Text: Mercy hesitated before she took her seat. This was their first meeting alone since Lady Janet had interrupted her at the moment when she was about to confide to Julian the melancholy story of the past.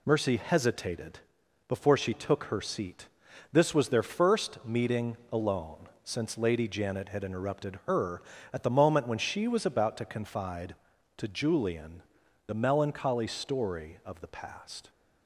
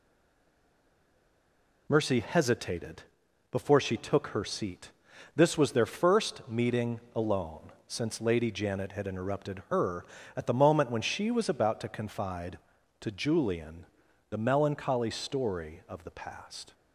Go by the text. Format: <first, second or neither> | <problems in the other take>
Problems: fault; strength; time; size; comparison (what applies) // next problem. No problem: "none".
first | stays silent before the first word; noticeable; until 1.8 s; 1.8 s long // pauses between "hesitated" and "before"; noticeable; at 3.0 s; 0.48 s long; noticeable in the first // pauses between "meeting" and "alone"; slight; at 6.9 s; 0.16 s long; slight in the first // pauses between "alone" and "since"; slight; at 7.7 s; 0.16 s long; slight in the first // pauses between "Julian" and "the"; at 13.8 s; 0.44 s long; also in the first